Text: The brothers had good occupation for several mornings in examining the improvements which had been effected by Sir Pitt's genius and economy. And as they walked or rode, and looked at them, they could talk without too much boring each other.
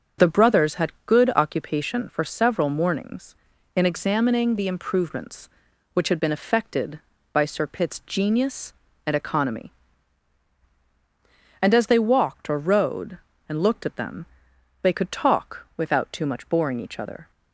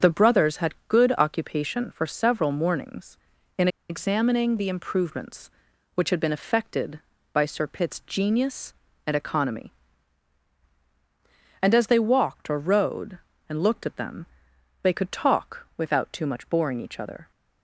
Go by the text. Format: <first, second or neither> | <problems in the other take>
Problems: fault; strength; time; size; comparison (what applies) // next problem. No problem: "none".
first | starts louder than the rest; until 1.1 s; 6.5 dB; also in the first // pauses between "in" and "examining"; slight; at 3.6 s; 0.22 s long